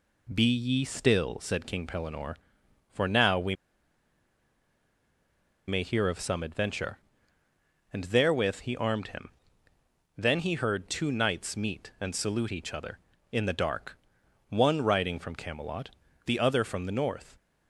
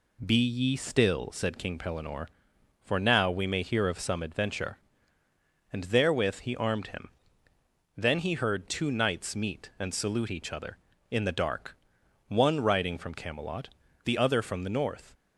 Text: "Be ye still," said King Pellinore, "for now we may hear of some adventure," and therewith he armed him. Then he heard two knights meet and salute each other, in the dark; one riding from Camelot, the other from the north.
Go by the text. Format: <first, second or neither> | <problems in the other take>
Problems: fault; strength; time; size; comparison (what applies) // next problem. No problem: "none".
second | pauses between "we" and "may"; strong; at 3.5 s; 2.1 s long